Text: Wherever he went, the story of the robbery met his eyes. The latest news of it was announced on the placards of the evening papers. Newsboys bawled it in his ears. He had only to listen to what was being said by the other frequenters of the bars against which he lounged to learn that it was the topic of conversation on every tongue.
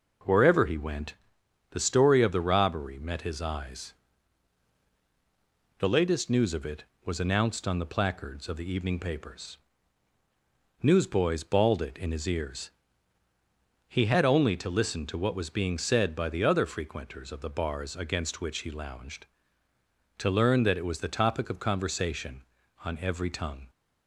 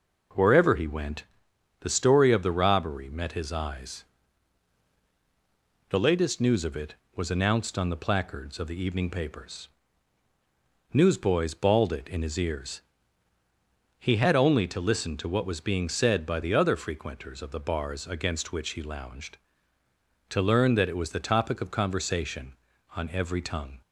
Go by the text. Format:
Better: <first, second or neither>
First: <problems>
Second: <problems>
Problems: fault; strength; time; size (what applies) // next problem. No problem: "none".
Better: neither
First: none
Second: none